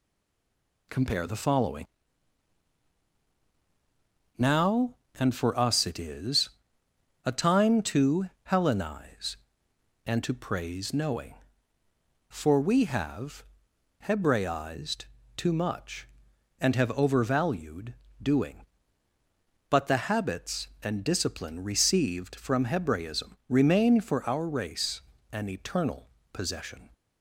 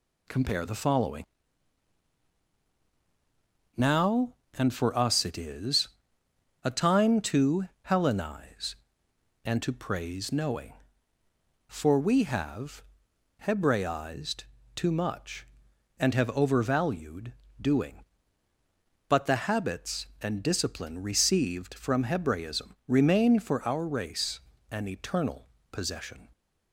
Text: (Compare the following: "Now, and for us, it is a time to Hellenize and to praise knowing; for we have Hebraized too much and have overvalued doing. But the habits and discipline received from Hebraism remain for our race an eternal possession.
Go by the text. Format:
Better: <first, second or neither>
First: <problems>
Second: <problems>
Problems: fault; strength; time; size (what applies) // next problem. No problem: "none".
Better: second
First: stays silent before the first word; slight; until 0.8 s; 0.8 s long // pauses between "is" and "a"; noticeable; at 6.4 s; 0.76 s long // pauses between "to" and "Hellenize"; slight; at 8.2 s; 0.18 s long // pauses between "have" and "Hebraized"; noticeable; at 13.4 s; 0.58 s long // pauses between "Hebraized" and "too"; slight; at 15.0 s; 0.32 s long // pauses between "overvalued" and "doing"; slight; at 17.9 s; 0.28 s long // pauses between "race" and "an"; slight; at 25.0 s; 0.30 s long // pauses between "eternal" and "possession"; slight; at 26.0 s; 0.24 s long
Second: pauses between "is" and "a"; noticeable; at 5.8 s; 0.76 s long // pauses between "to" and "Hellenize"; slight; at 7.6 s; 0.18 s long // pauses between "have" and "Hebraized"; noticeable; at 12.8 s; 0.58 s long // pauses between "Hebraized" and "too"; slight; at 14.4 s; 0.32 s long // pauses between "overvalued" and "doing"; slight; at 17.3 s; 0.28 s long // pauses between "race" and "an"; slight; at 24.4 s; 0.30 s long // pauses between "eternal" and "possession"; slight; at 25.4 s; 0.24 s long